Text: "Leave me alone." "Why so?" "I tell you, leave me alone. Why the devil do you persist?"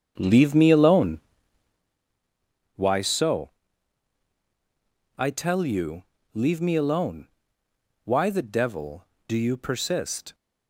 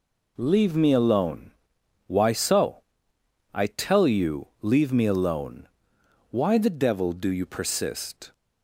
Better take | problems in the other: second | starts louder than the rest; strong; until 2.0 s; 7.5 dB

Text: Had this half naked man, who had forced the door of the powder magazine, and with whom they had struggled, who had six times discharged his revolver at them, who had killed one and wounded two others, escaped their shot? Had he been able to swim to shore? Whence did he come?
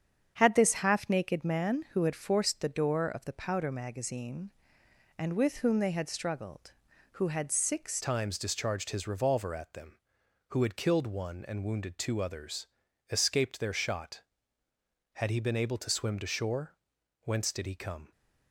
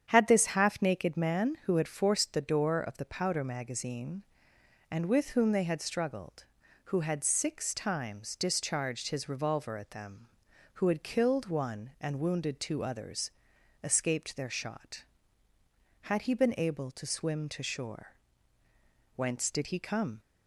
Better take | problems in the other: second | starts louder than the rest; strong; until 1.4 s; 8 dB; strong in the second // changes voice at "times"; from 8.0 s on; 10.1 s long

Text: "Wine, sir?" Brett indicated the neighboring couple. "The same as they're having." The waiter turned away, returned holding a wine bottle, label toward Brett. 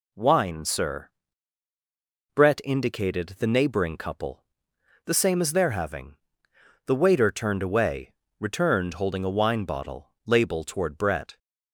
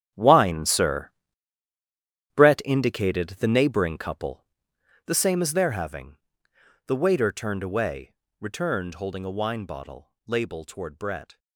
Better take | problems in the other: first | gets quieter; strong; throughout; 14.5 dB

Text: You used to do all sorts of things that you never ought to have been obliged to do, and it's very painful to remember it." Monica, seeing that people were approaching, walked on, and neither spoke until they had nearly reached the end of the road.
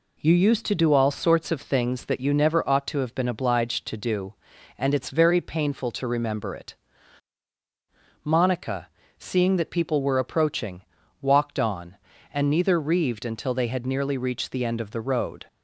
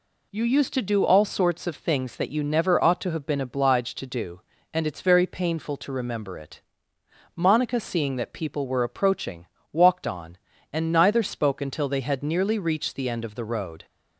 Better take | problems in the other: second | says "reaved" for "spoke"; at 12.8 s

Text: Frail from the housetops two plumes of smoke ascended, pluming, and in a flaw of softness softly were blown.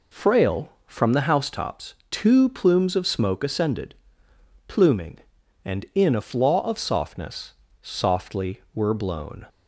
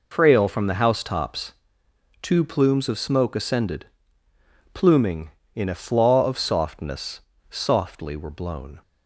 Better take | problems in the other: first | pauses between "housetops" and "two"; noticeable; at 1.5 s; 0.68 s long; slight in the first // skips "and"; at 5.4 s // pauses between "softness" and "softly"; slight; at 7.2 s; 0.28 s long; slight in the first

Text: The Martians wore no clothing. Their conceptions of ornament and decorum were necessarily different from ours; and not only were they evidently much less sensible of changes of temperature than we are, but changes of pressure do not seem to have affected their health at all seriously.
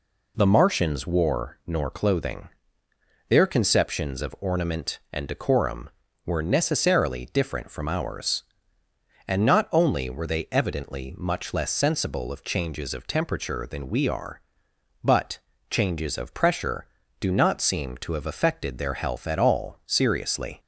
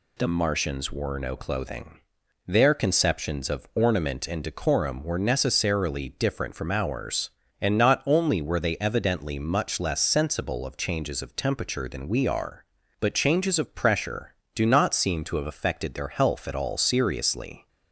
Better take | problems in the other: second | says "nor" for "no"; at 1.6 s // pauses between "but" and "changes"; slight; at 15.3 s; 0.32 s long

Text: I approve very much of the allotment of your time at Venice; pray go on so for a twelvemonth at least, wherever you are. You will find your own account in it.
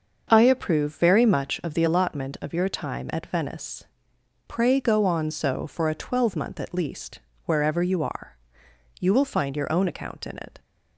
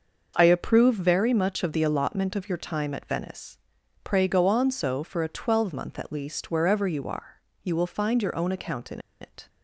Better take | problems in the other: first | starts louder than the rest; until 1.3 s; 6 dB; also in the first // pauses between "in" and "it"; slight; at 8.9 s; 0.22 s long

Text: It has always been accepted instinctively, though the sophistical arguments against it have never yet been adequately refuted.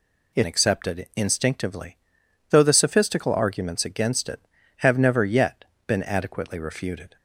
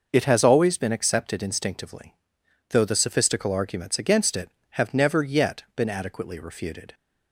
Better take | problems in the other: second | skips "has always been"; at 0.4 s // pauses between "yet" and "been"; slight; at 5.6 s; 0.24 s long

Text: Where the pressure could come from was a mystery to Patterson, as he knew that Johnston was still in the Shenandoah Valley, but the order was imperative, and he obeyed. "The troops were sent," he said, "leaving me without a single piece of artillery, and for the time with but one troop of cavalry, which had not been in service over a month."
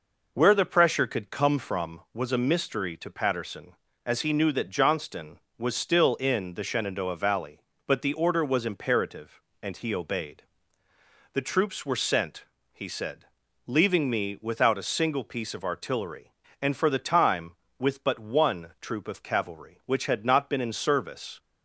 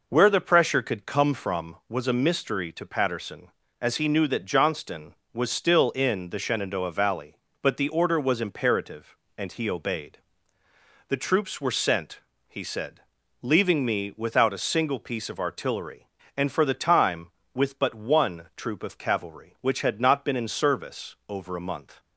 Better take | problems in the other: second | stops before "over a month"; at 21.3 s

